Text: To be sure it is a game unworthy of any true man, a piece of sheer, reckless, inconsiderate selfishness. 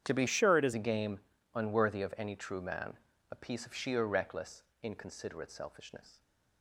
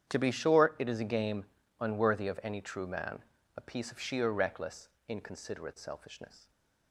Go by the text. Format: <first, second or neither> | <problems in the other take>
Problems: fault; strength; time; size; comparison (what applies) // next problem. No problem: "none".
second | starts louder than the rest; strong; until 1.0 s; 9 dB; strong in the second // changes voice from "sure" to "is"; from 0.2 to 0.7 s; 0.5 s long // pauses between "game" and "unworthy"; at 1.1 s; 0.38 s long; also in the second